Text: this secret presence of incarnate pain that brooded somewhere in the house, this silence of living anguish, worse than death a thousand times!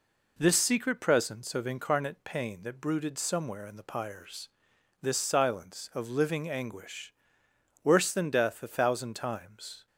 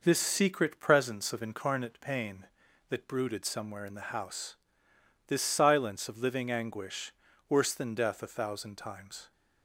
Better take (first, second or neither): second